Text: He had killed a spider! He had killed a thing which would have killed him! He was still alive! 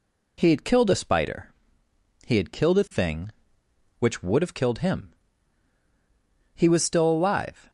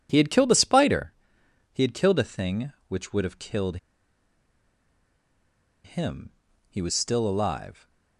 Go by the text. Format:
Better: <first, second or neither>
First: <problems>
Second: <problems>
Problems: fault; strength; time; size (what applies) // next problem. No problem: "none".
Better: first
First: none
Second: pauses between "killed" and "him"; strong; at 3.7 s; 2.0 s long